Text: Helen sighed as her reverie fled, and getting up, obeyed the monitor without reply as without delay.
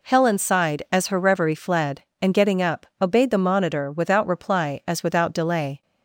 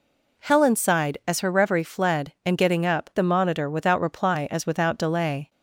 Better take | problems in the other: first | skips "obeyed"; at 3.1 s

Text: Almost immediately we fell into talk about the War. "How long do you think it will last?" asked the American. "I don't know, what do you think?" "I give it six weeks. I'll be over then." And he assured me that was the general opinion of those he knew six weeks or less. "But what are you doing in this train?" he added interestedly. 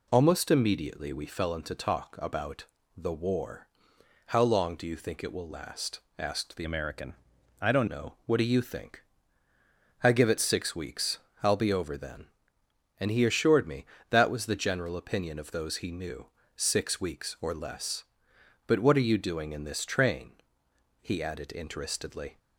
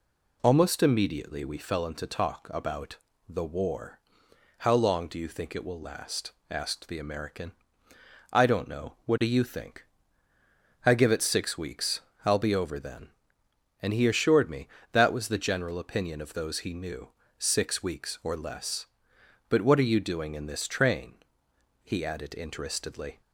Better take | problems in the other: second | pauses between "about" and "the"; slight; at 2.6 s; 0.32 s long; slight in the second // changes voice from "American" to "don't"; from 6.6 to 7.8 s; 1.2 s long // pauses between "knew" and "six"; slight; at 16.2 s; 0.28 s long; slight in the second

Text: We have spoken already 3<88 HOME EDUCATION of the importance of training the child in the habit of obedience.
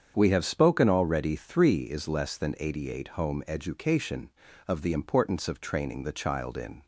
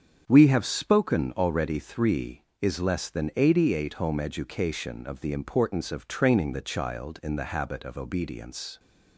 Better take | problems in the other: second | starts louder than the rest; strong; until 1.1 s; 7.5 dB; strong in the second // stops before "the habit of obedience"; at 6.8 s

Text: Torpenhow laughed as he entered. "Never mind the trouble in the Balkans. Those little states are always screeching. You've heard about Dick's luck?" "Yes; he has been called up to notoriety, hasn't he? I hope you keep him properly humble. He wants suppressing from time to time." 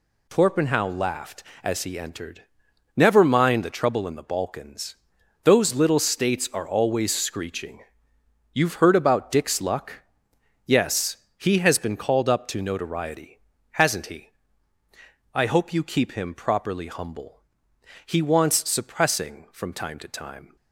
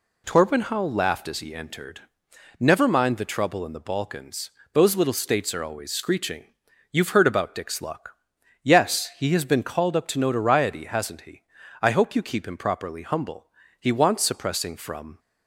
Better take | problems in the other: first | stops before "time to time"; at 15.1 s

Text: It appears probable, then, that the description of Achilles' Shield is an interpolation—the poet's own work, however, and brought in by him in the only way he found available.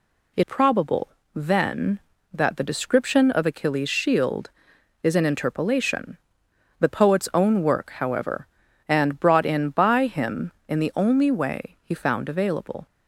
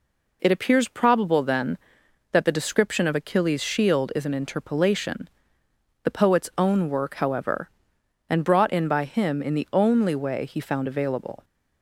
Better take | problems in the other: second | skips "appears"; at 0.4 s

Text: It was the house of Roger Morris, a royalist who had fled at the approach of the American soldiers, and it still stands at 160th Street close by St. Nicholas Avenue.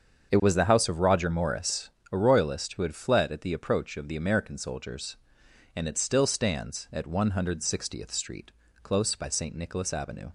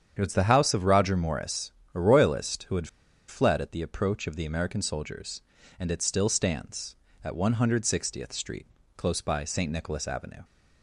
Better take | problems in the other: first | starts louder than the rest; strong; until 1.1 s; 8.5 dB; strong in the first // pauses between "had" and "fled"; at 2.8 s; 0.40 s long // pauses between "Street" and "close"; slight; at 8.6 s; 0.30 s long; slight in the first

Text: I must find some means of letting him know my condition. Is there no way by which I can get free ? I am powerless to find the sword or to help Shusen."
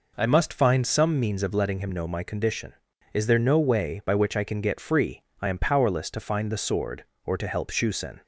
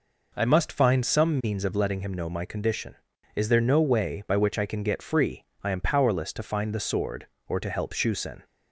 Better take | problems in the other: neither | none

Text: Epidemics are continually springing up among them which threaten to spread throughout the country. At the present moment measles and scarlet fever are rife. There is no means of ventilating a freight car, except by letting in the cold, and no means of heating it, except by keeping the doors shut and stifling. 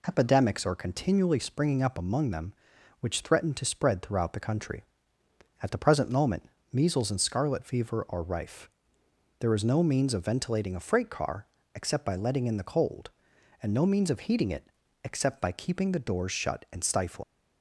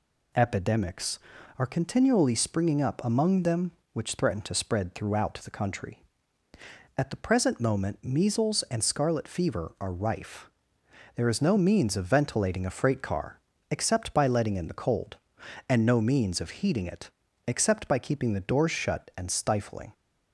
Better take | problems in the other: second | pauses between "moment" and "measles"; slight; at 6.4 s; 0.28 s long // leaves "stifling" unfinished; at 17.2 s; 90 ms

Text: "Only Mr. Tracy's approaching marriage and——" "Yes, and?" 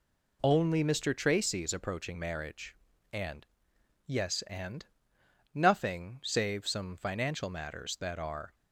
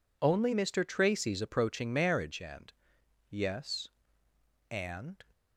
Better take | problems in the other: second | goes on to say "Nothing save some financial matters that are"; strong; from 5.5 s on; 3.0 s long

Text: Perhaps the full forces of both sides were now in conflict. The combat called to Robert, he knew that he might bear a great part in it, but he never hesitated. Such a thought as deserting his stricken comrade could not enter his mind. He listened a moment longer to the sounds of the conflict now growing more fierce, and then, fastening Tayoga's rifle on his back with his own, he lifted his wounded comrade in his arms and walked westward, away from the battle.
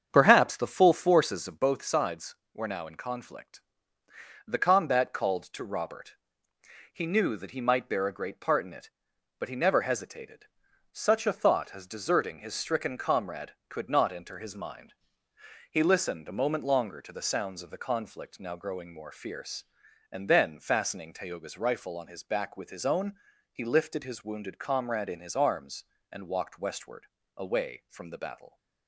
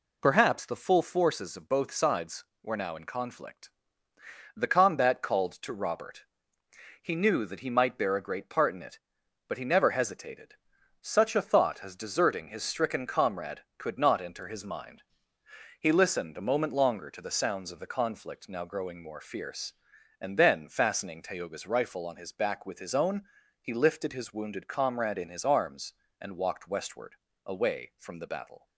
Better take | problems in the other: second | starts louder than the rest; strong; until 1.8 s; 7.5 dB

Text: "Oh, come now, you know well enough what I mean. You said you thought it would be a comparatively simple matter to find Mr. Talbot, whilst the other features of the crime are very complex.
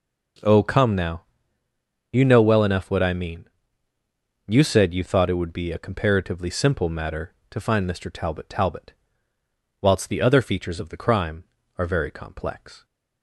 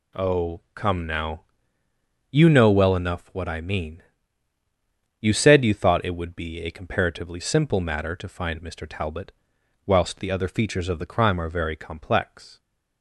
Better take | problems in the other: second | says "Talbot" twice; at 8.4 s

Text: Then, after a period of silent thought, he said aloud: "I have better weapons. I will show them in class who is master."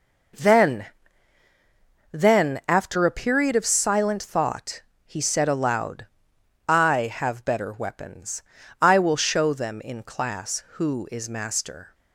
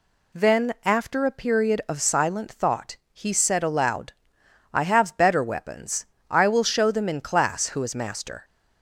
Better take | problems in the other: second | says "Then" twice; at 2.1 s

